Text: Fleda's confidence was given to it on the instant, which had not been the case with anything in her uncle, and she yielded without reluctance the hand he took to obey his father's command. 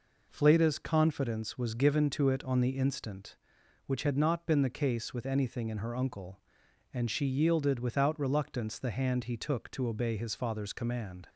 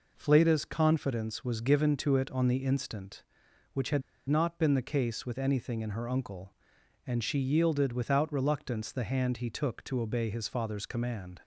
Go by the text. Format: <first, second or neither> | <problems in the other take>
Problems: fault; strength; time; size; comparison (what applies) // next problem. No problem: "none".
first | pauses between "had" and "not"; slight; at 4.0 s; 0.28 s long